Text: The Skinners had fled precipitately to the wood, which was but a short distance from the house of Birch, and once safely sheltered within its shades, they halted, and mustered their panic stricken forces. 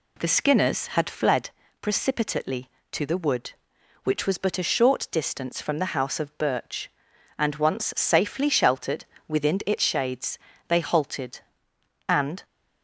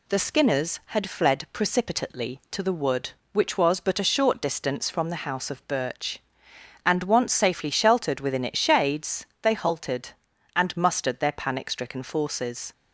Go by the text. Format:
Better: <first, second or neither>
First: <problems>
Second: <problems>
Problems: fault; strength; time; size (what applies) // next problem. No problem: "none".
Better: second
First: pauses between "fled" and "precipitately"; slight; at 1.5 s; 0.28 s long // pauses between "sheltered" and "within"; slight; at 9.0 s; 0.22 s long // stops before "mustered their panic stricken forces"; at 12.4 s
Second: none